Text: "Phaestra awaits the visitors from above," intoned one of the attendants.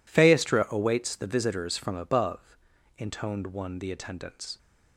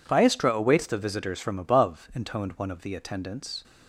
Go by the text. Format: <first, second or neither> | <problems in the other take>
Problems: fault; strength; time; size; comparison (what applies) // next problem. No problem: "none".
second | skips "of"; at 3.7 s